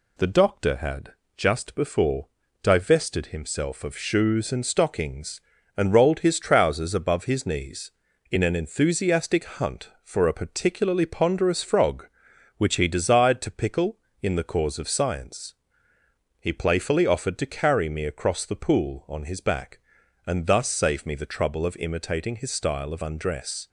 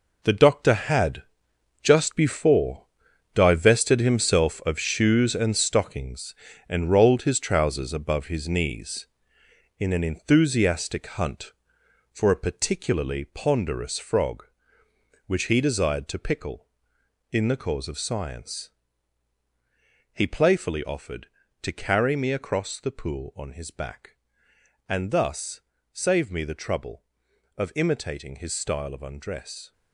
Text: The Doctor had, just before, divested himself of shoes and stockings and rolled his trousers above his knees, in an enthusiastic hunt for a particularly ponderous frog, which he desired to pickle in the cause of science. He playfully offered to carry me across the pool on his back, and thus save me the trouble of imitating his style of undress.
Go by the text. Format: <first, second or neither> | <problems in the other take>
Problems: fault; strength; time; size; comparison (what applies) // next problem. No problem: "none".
first | gets quieter; strong; throughout; 10.5 dB // pauses between "thus" and "save"; slight; at 25.6 s; 0.32 s long